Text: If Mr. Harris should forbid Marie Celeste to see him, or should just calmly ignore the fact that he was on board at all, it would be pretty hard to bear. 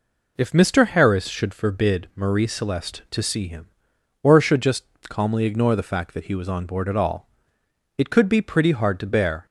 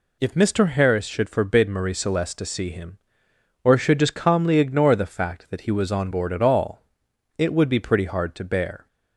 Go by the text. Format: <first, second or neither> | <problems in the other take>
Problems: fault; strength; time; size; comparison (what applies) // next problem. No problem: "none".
second | pauses between "just" and "calmly"; slight; at 4.8 s; 0.24 s long // says "could" for "would"; at 8.1 s